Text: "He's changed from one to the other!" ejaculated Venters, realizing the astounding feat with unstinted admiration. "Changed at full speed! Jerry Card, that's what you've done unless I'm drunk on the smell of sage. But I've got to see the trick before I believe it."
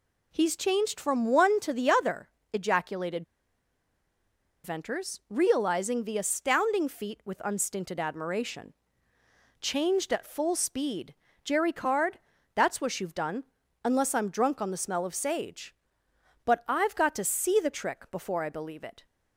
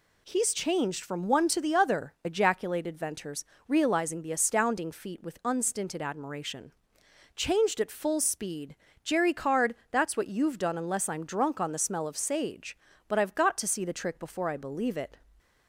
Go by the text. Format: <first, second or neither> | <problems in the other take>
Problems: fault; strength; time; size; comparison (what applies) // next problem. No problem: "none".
second | pauses between "ejaculated" and "Venters"; strong; at 3.2 s; 1.4 s long // pauses between "done" and "unless"; at 13.4 s; 0.40 s long